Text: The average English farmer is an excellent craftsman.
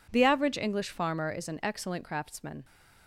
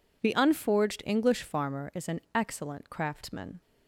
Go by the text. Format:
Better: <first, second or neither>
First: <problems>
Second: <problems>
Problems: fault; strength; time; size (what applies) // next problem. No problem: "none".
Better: first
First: none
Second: says "unforged" for "average"; at 0.3 s